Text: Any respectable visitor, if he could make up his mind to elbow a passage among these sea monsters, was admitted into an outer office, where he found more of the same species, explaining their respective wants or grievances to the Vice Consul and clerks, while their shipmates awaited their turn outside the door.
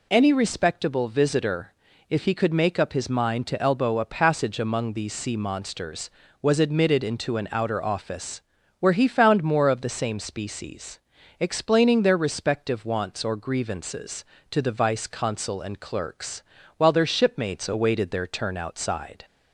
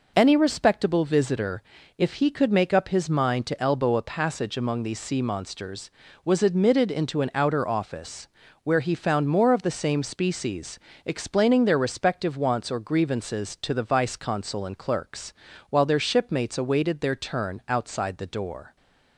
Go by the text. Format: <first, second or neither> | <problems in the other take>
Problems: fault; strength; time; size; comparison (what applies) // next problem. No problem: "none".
second | stops before "the door"; at 19.2 s